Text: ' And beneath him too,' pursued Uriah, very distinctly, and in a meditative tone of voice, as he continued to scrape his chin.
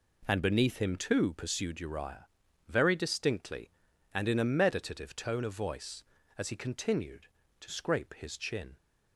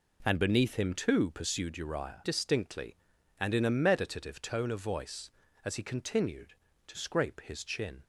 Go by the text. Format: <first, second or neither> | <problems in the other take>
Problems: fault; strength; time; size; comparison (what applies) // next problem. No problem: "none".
first | skips "very"; at 2.2 s